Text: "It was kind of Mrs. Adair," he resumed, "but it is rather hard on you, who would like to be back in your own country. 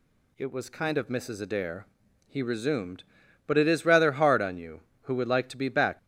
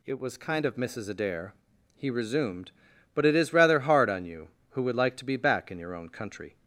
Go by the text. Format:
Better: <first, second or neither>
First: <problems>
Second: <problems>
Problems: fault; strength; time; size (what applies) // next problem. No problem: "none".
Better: second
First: stops before "in your own country"; at 5.9 s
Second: none